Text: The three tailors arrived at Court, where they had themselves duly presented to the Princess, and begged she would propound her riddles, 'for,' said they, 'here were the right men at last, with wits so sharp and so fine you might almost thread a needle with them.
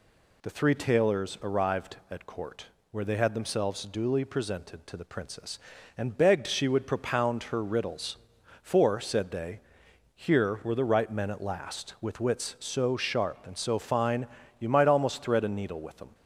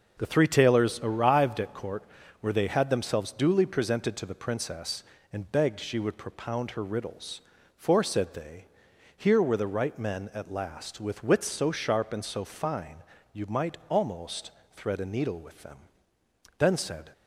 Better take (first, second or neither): first